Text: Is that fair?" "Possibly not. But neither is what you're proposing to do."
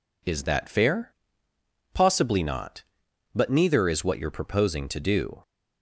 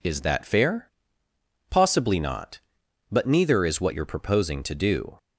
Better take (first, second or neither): neither